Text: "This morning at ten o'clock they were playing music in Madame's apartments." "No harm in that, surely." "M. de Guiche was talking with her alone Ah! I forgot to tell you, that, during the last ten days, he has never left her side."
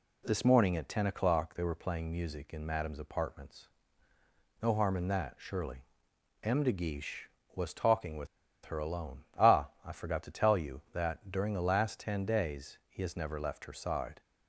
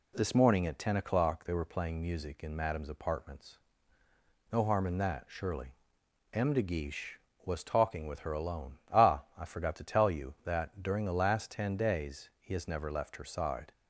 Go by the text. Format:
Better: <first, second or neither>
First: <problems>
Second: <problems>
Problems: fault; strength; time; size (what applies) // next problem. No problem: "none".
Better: second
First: pauses between "with" and "her"; at 8.2 s; 0.38 s long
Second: none